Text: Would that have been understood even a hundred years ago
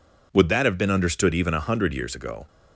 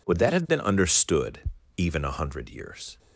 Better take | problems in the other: first | pauses between "understood" and "even"; slight; at 1.4 s; 0.36 s long // stops before "ago"; at 2.9 s

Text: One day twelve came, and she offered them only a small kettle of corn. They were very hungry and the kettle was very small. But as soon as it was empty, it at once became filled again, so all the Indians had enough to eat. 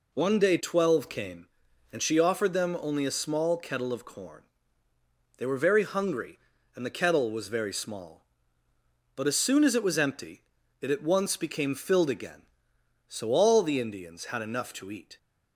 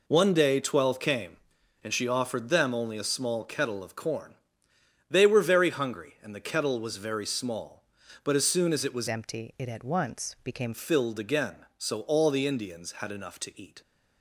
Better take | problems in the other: first | changes voice from "empty" to "became"; from 9.0 to 10.7 s; 1.7 s long

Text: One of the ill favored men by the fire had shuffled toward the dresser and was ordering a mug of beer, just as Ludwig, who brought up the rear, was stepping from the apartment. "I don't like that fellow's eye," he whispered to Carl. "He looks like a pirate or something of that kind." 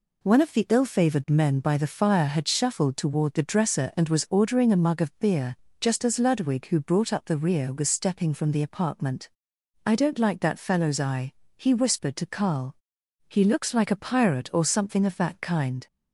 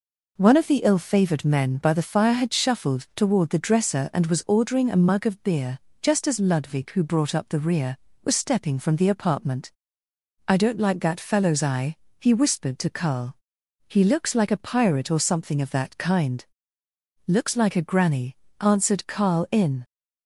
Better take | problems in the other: first | goes on to say "Looks like a granny answered Carl in"; strong; from 17.2 s on; 2.5 s long

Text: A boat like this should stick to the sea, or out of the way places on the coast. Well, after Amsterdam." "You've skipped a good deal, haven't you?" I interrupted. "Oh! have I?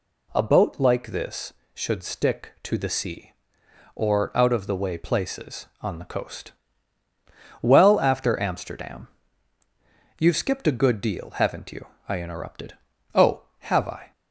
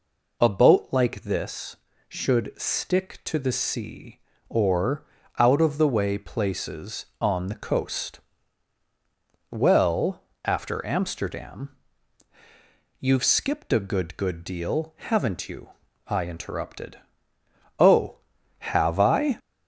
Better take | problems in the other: first | pauses between "or" and "out"; slight; at 5.0 s; 0.34 s long // says "good" twice; at 14.1 s

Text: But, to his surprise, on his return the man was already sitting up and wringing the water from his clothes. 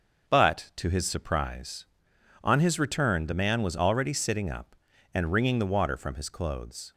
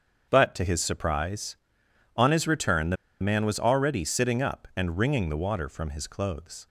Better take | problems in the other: first | starts louder than the rest; strong; until 1.3 s; 7 dB; also in the first // pauses between "the" and "man"; slight; at 2.9 s; 0.27 s long

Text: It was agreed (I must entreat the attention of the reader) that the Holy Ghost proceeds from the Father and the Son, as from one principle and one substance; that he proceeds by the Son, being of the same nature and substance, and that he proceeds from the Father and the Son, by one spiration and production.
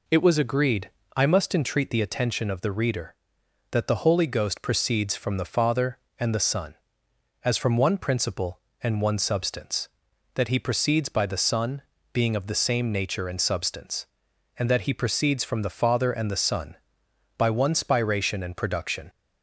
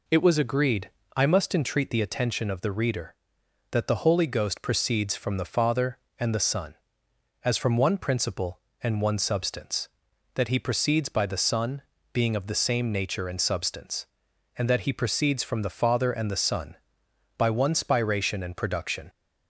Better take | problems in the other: neither | none

